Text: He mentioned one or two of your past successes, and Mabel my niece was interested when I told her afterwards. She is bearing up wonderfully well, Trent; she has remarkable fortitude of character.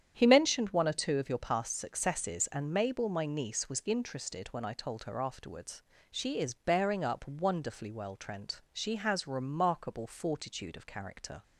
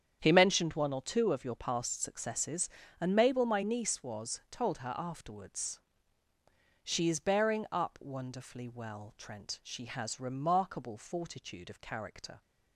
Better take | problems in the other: first | starts louder than the rest; strong; until 1.2 s; 8 dB; strong in the first // skips "interested when I"; at 4.4 s

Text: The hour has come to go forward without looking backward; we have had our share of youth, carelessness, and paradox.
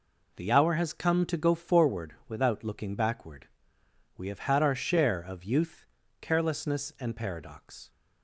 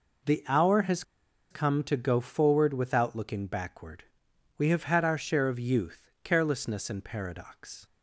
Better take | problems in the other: first | pauses between "has" and "come"; noticeable; at 1.0 s; 0.48 s long

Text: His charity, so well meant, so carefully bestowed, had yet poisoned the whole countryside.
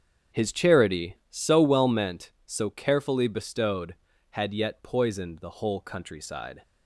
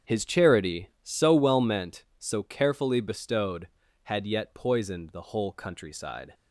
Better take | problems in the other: neither | starts louder than the rest; strong; the same in both

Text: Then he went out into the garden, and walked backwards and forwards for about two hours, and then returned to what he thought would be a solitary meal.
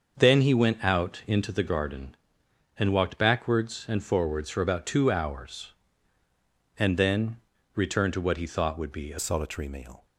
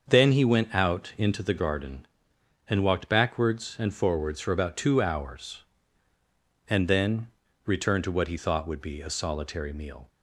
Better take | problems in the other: second | starts louder than the rest; until 1.1 s; 6.5 dB; also in the second // pauses between "then" and "returned"; at 7.3 s; 0.38 s long; also in the second // changes voice at "solitary"; from 9.1 s on; 0.9 s long

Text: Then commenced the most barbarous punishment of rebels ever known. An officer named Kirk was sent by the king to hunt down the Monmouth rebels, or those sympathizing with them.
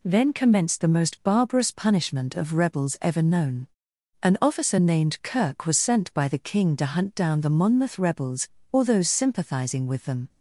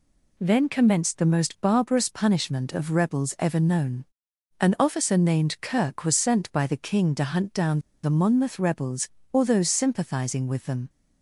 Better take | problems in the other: first | pauses between "down" and "the"; slight; at 7.7 s; 0.24 s long

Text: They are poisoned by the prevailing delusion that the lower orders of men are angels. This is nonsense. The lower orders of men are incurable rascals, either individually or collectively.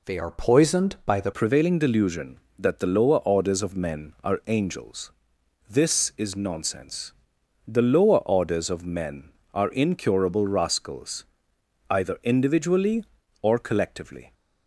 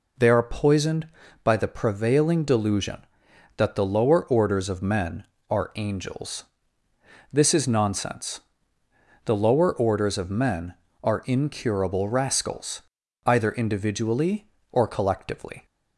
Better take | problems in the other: second | changes voice at "prevailing"; from 1.3 s on; 13.0 s long

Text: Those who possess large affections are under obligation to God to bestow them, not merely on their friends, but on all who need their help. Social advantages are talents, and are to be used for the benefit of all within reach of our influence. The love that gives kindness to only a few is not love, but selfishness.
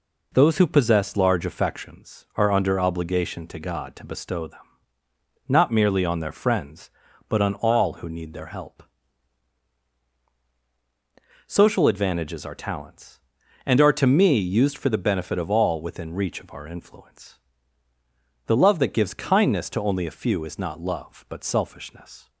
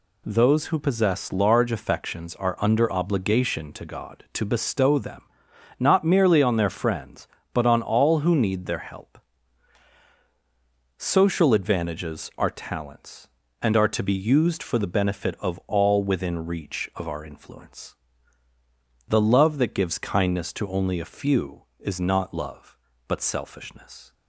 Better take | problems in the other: second | says "me" for "be"; at 14.0 s

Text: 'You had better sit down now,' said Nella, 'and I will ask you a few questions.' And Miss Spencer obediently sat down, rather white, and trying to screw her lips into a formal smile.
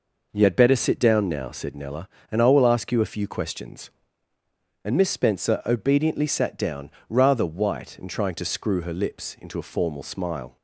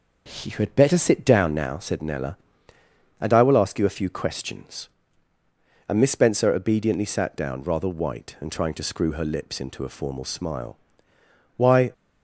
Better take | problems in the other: first | starts louder than the rest; until 1.4 s; 6.5 dB // goes on to say "Why"; slight; from 11.5 s on; 0.34 s long

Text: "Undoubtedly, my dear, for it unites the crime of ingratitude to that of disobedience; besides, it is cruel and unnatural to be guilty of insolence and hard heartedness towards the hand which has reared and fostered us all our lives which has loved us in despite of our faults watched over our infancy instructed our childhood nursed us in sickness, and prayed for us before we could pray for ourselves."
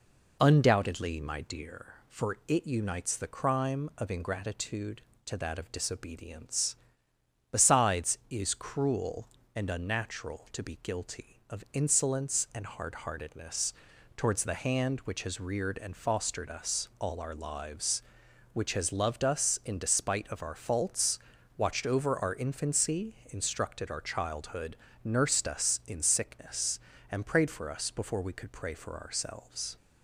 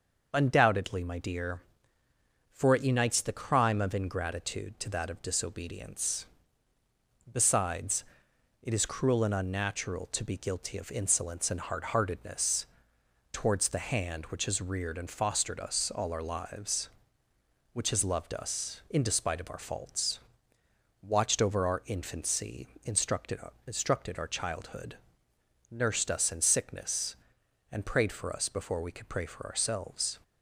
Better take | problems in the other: first | starts louder than the rest; noticeable; until 1.3 s; 6 dB // pauses between "heartedness" and "towards"; noticeable; at 12.6 s; 0.66 s long; also in the first // pauses between "faults" and "watched"; noticeable; at 20.1 s; 0.84 s long; also in the first // pauses between "infancy" and "instructed"; slight; at 22.6 s; 0.16 s long // says "instructed" twice; at 23.6 s // pauses between "childhood" and "nursed"; noticeable; at 24.9 s; 0.74 s long; slight in the first

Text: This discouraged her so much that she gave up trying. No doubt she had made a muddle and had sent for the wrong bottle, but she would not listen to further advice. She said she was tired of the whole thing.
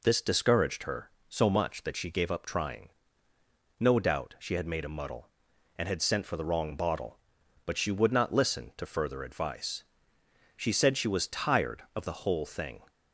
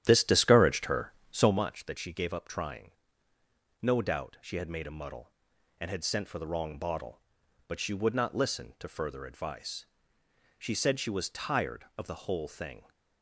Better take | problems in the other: first | starts louder than the rest; strong; until 1.5 s; 11 dB

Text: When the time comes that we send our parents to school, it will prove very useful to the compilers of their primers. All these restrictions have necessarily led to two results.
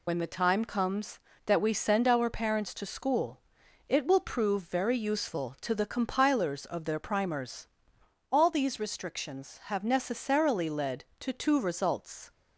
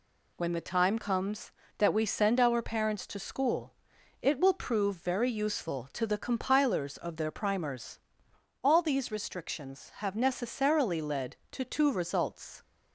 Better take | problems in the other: second | loses the start of "When"; at 0.0 s; 55 ms

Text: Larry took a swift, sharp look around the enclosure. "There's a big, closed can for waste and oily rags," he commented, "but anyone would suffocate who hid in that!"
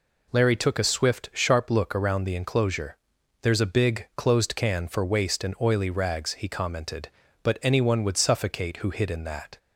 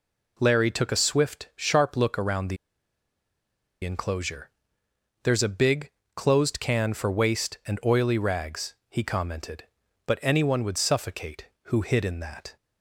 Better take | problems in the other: first | pauses between "the" and "enclosure"; strong; at 2.5 s; 1.2 s long

